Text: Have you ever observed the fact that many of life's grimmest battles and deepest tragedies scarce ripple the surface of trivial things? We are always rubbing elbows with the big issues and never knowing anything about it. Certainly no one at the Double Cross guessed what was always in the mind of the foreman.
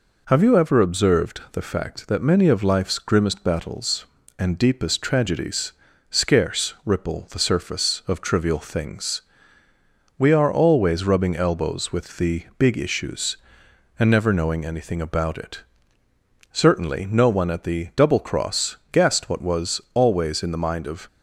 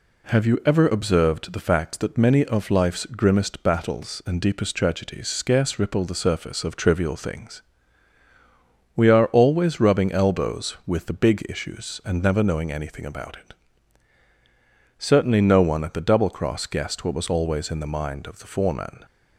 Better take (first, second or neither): second